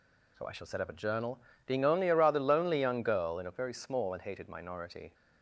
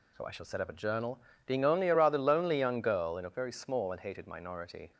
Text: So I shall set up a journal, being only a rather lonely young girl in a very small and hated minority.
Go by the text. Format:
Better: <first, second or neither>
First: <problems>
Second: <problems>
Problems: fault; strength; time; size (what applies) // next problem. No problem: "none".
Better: neither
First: none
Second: none